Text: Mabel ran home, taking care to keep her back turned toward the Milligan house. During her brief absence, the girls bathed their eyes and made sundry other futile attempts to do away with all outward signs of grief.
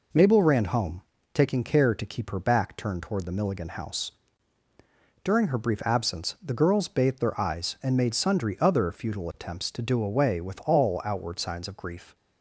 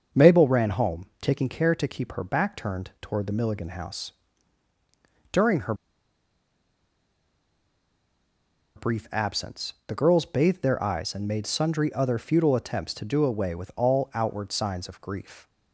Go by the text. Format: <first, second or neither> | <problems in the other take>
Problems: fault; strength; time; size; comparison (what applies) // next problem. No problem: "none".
first | starts louder than the rest; until 1.3 s; 6.5 dB // pauses between "her" and "brief"; strong; at 5.7 s; 3.0 s long